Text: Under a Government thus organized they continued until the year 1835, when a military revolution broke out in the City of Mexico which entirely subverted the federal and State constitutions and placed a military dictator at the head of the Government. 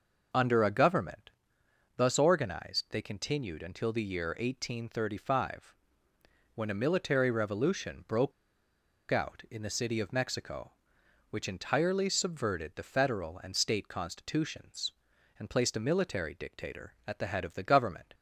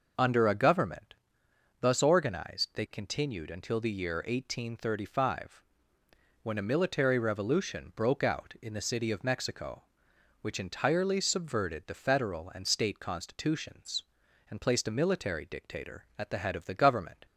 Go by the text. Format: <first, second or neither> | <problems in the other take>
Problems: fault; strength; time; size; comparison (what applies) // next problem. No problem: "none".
second | pauses between "Government" and "thus"; noticeable; at 1.2 s; 0.68 s long; noticeable in the second // pauses between "broke" and "out"; noticeable; at 8.3 s; 0.77 s long